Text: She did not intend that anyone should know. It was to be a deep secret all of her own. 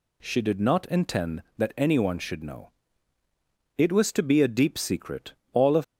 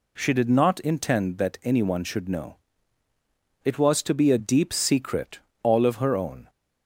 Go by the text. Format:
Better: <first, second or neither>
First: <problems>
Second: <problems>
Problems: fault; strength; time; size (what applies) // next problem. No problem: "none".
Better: second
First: pauses between "secret" and "all"; slight; at 5.3 s; 0.18 s long // stops before "her own"; at 5.8 s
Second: pauses between "secret" and "all"; slight; at 5.3 s; 0.24 s long